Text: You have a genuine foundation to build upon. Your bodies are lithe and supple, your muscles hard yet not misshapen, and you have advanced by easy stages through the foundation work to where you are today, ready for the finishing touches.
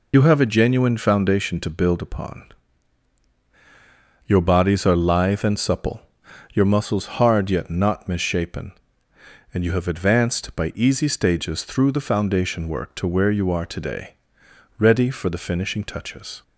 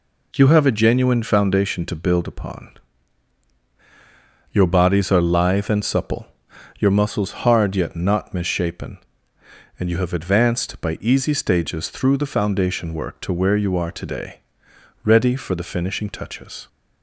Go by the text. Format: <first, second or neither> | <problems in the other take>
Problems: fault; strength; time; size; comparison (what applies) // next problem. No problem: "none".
second | loses the start of "You"; at 0.1 s; 55 ms